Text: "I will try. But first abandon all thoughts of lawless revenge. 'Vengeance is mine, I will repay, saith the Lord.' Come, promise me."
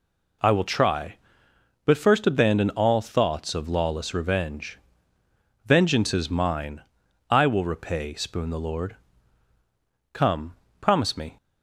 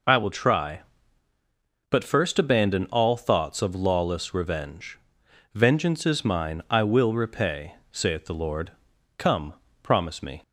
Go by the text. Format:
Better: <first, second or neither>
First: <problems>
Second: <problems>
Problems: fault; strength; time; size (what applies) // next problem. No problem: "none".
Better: second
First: says "spoon" for "saith"; at 8.1 s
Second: none